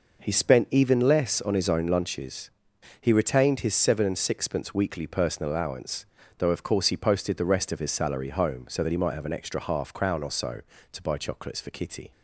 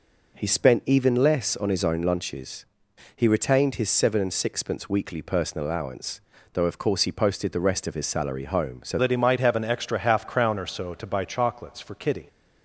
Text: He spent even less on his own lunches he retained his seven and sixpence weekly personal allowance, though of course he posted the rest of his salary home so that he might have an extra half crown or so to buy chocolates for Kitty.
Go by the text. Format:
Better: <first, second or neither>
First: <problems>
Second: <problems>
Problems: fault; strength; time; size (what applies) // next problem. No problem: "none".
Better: first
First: pauses between "lunches" and "he"; noticeable; at 2.4 s; 0.50 s long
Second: pauses between "lunches" and "he"; noticeable; at 2.6 s; 0.50 s long // changes voice at "that"; from 8.9 s on; 3.3 s long